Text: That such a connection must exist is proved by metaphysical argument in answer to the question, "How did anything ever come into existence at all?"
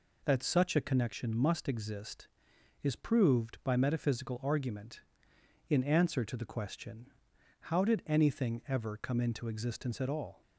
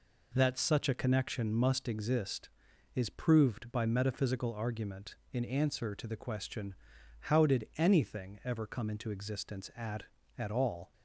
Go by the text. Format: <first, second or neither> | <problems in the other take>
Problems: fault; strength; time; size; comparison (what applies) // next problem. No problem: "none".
first | says "at" twice; at 10.3 s